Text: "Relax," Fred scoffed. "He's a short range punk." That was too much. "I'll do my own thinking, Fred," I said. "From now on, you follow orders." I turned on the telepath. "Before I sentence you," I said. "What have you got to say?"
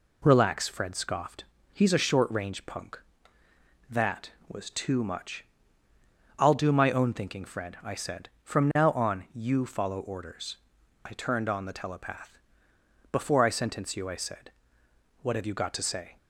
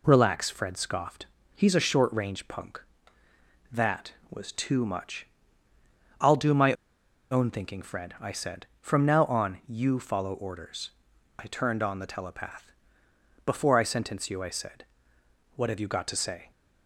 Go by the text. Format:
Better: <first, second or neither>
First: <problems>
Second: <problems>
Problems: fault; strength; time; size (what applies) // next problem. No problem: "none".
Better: first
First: none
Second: pauses between "my" and "own"; noticeable; at 6.7 s; 0.57 s long